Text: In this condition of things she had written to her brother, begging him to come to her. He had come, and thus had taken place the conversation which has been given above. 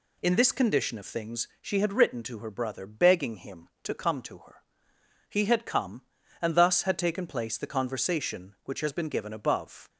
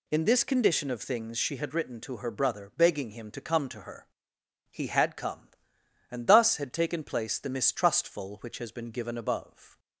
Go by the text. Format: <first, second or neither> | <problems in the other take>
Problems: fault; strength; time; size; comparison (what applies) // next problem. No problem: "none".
first | says "mistrustful" for "conversation"; at 7.4 s